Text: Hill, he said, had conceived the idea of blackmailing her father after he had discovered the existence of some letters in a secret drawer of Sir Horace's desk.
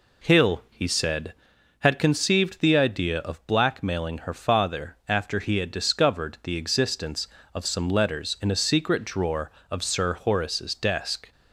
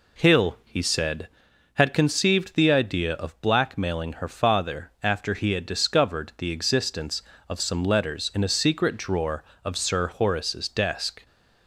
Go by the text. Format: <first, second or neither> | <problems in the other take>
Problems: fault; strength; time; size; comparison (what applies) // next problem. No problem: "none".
neither | none